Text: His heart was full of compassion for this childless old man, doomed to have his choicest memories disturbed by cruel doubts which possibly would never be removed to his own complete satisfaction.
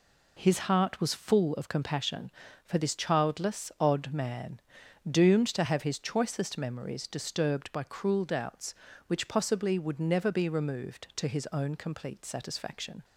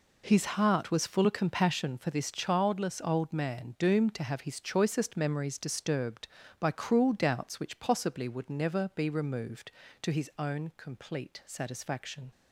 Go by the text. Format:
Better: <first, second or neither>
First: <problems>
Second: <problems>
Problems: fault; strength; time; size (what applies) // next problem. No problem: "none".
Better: second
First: says "odd" for "old"; at 3.7 s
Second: none